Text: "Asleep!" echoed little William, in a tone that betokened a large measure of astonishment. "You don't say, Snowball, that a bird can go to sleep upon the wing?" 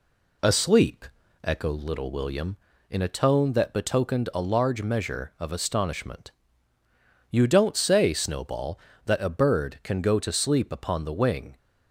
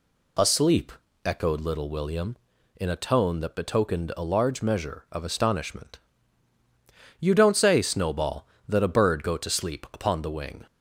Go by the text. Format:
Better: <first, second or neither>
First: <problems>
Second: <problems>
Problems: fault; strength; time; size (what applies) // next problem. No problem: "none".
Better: first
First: none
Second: skips "can"; at 9.2 s